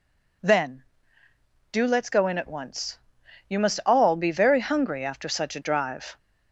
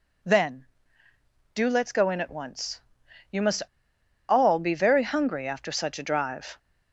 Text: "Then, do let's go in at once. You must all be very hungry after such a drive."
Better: first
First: none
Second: pauses between "must" and "all"; noticeable; at 3.6 s; 0.64 s long

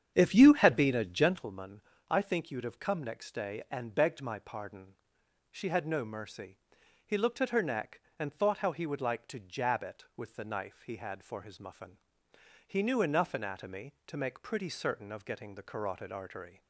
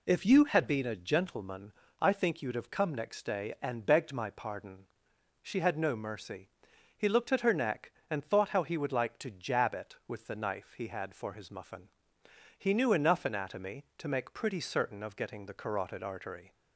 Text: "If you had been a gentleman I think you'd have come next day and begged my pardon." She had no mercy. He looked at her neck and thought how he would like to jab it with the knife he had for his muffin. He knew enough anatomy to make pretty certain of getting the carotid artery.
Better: second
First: starts louder than the rest; strong; until 1.5 s; 8.5 dB // pauses between "gentleman" and "I"; slight; at 1.8 s; 0.28 s long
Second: pauses between "gentleman" and "I"; slight; at 1.7 s; 0.28 s long

